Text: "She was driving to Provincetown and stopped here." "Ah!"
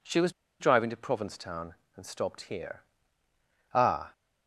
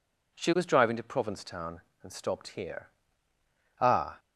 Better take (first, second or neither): second